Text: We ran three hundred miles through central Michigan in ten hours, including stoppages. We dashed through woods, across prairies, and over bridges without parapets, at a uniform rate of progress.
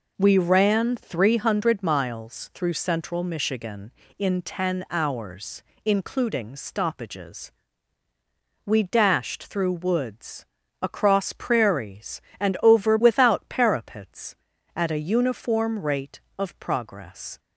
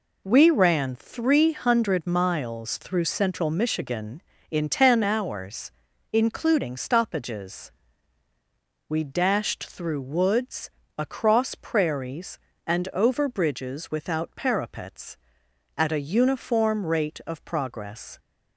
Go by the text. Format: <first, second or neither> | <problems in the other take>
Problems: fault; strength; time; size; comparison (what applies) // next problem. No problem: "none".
second | skips "bridges"; at 12.9 s